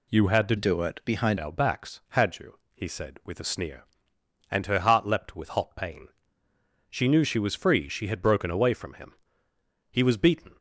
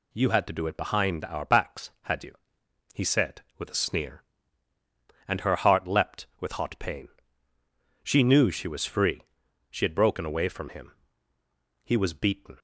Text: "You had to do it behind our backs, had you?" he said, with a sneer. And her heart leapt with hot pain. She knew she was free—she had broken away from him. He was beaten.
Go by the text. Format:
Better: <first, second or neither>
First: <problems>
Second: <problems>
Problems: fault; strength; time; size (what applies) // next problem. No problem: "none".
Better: second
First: changes voice from "do" to "behind"; from 0.5 to 1.3 s; 0.8 s long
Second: none